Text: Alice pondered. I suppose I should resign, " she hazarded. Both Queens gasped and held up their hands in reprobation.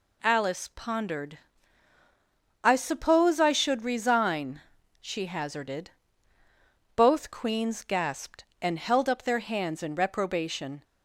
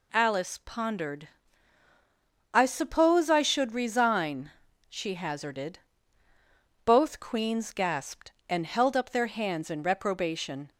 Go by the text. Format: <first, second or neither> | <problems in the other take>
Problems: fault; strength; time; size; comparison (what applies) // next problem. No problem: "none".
neither | none